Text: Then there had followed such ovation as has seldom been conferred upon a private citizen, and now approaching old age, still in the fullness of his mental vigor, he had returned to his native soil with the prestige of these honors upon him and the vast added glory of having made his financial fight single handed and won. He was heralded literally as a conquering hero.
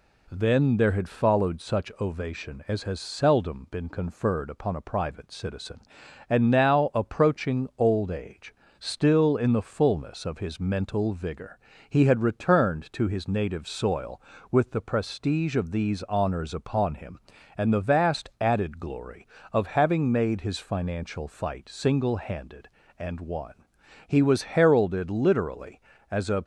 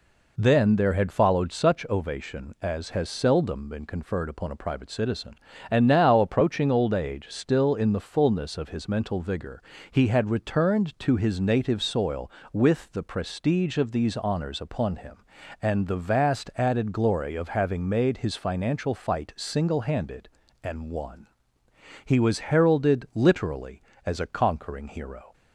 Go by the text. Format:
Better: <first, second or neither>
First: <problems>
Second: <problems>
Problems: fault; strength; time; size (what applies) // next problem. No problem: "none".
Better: second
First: stops before "conquering hero"; at 26.4 s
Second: none